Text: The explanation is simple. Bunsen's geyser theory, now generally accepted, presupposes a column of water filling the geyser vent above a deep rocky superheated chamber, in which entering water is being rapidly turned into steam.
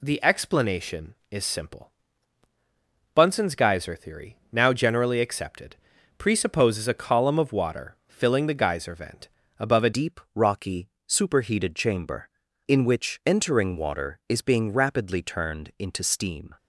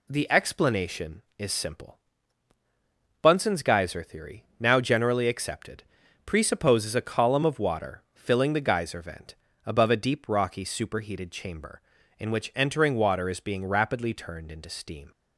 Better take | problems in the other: second | pauses between "vent" and "above"; slight; at 9.2 s; 0.30 s long; slight in the second // changes voice at "deep"; from 9.9 s on; 6.6 s long // pauses between "rocky" and "superheated"; slight; at 10.9 s; 0.16 s long

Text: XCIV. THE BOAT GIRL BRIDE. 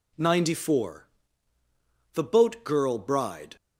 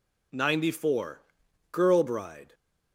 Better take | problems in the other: first | skips "THE BOAT"; at 1.4 s

